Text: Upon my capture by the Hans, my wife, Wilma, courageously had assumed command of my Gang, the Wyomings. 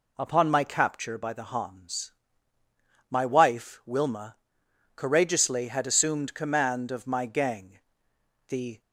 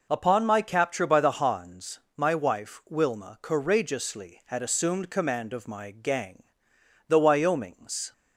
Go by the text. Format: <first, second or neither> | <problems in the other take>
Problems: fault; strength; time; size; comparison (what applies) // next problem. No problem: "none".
second | stops before "Wyomings"; at 8.8 s